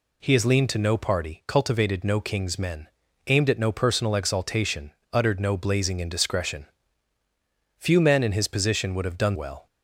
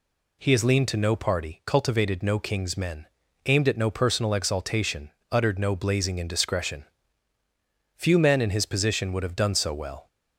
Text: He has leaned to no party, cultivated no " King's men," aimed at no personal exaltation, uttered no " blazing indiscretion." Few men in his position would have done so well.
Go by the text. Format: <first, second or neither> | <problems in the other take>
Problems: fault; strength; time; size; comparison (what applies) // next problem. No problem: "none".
second | skips "so"; at 9.3 s